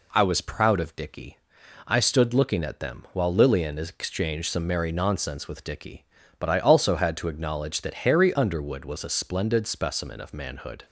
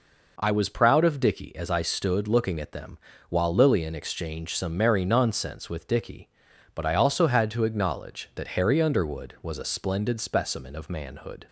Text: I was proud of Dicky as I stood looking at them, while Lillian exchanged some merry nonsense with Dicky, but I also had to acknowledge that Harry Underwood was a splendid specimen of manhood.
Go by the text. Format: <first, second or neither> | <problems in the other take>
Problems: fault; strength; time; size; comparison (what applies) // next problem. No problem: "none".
second | skips "as"; at 1.6 s